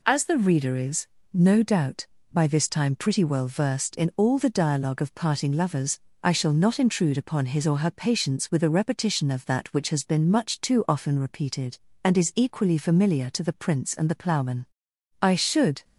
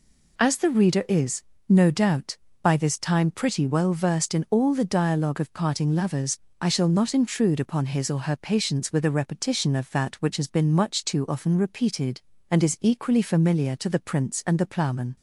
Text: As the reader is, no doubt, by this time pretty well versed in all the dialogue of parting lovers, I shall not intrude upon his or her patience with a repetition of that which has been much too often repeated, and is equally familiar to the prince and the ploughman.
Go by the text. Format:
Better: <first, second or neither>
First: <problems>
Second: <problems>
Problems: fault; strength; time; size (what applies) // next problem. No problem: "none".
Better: second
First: goes on to say "I should"; noticeable; from 15.2 s on; 0.62 s long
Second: none